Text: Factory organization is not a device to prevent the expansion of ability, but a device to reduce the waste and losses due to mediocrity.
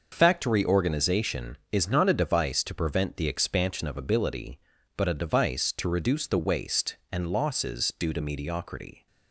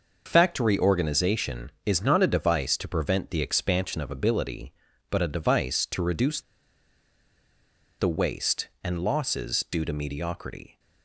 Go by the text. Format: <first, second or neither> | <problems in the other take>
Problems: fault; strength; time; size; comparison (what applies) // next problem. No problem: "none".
first | pauses between "reduce" and "the"; strong; at 6.4 s; 1.5 s long